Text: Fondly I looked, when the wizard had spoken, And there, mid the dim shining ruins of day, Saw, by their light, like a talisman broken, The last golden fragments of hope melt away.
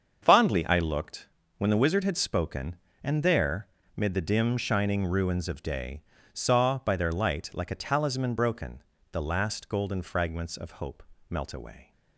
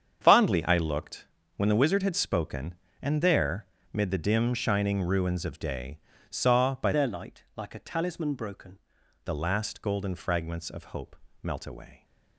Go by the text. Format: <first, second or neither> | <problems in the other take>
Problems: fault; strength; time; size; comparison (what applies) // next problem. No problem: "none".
first | starts louder than the rest; strong; until 1.2 s; 8 dB; also in the first // changes voice from "their" to "broken"; from 6.9 to 8.7 s; 1.8 s long // pauses between "hope" and "melt"; slight; at 11.1 s; 0.26 s long; slight in the first